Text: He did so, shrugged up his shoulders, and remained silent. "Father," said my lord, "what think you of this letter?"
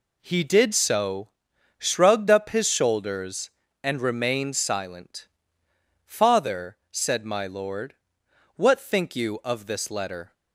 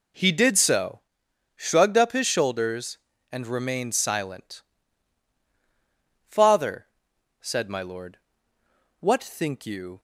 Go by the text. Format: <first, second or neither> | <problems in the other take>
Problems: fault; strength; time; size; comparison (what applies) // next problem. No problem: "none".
first | stops before "of this letter"; at 9.9 s